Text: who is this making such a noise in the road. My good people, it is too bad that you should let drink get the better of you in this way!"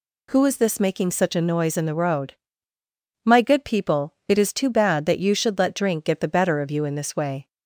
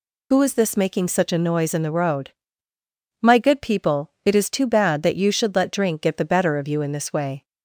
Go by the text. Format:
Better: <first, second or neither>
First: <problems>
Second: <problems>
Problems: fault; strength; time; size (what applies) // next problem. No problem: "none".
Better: first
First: none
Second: loses the start of "who"; at 0.3 s; 50 ms